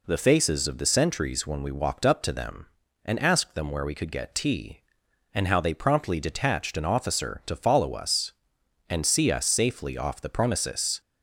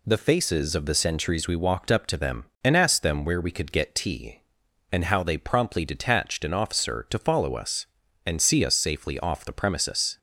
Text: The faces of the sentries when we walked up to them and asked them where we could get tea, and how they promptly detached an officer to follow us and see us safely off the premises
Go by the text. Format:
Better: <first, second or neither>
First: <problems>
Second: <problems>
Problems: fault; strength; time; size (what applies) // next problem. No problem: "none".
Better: first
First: none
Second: skips "when"; at 1.4 s